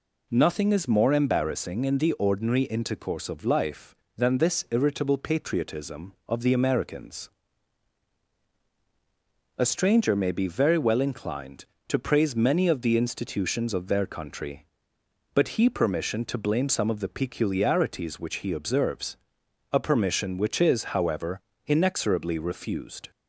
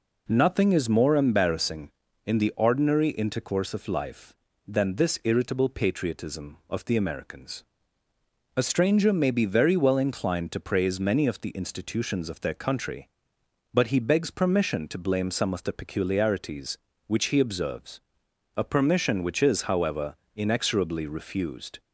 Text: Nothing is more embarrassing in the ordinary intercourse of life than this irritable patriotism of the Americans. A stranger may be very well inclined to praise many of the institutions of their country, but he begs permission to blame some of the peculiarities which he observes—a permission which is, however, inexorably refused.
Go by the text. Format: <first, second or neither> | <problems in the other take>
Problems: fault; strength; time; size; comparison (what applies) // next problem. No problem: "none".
second | skips "begs"; at 15.7 s